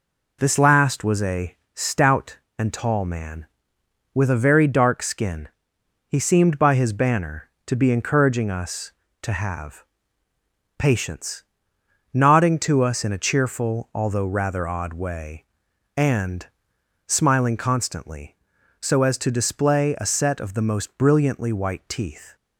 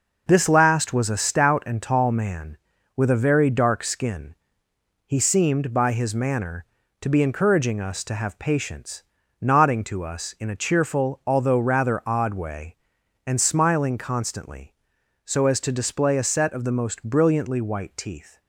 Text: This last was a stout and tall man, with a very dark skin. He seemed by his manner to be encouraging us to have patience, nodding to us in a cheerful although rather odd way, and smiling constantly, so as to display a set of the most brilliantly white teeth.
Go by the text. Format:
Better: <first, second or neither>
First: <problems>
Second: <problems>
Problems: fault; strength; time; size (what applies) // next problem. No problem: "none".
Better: second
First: pauses between "a" and "stout"; slight; at 1.5 s; 0.18 s long // says "banner" for "manner"; at 6.9 s // pauses between "have" and "patience"; noticeable; at 9.8 s; 0.94 s long // pauses between "and" and "smiling"; noticeable; at 16.4 s; 0.60 s long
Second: none